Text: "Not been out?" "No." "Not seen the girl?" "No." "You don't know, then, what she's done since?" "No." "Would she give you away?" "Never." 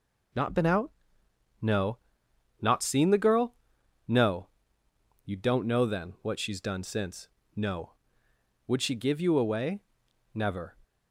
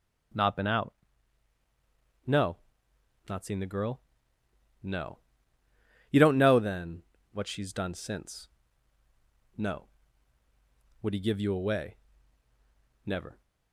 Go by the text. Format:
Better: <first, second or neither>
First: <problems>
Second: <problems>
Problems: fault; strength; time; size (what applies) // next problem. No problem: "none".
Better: first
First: none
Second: starts louder than the rest; strong; until 3.3 s; 8 dB // says "he" for "she"; at 11.1 s